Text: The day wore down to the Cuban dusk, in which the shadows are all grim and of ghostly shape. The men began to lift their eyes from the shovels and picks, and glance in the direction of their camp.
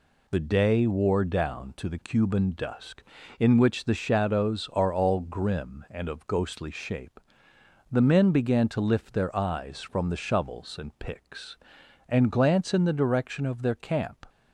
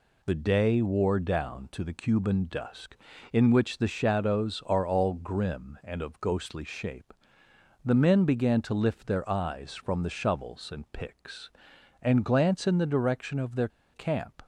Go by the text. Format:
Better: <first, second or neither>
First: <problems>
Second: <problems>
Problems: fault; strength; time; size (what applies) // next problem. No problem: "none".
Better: first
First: none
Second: pauses between "their" and "camp"; slight; at 13.6 s; 0.25 s long